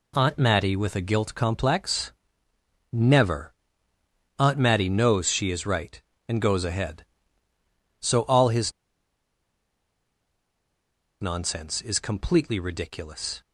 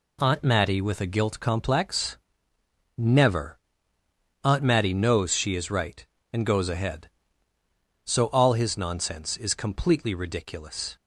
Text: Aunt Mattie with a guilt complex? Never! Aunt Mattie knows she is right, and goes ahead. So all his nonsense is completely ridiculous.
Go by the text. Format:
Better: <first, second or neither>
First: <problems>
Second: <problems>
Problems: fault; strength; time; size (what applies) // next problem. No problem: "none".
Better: second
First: pauses between "his" and "nonsense"; strong; at 8.7 s; 2.4 s long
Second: none